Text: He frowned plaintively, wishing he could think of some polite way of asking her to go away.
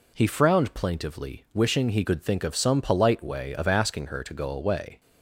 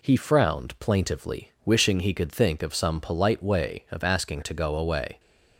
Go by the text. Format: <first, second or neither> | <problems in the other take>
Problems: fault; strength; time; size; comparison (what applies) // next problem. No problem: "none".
first | skips "her"; at 4.4 s